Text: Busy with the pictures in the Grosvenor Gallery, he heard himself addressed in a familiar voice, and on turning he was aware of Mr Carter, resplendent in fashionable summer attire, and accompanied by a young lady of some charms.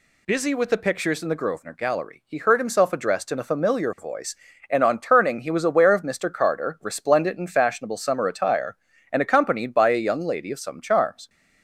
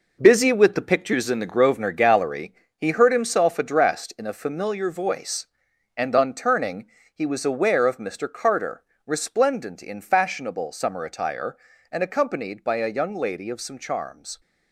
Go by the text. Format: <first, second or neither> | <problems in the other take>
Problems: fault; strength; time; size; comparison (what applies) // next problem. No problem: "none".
first | gets quieter; strong; throughout; 8.5 dB // pauses between "turning" and "he"; slight; at 6.8 s; 0.26 s long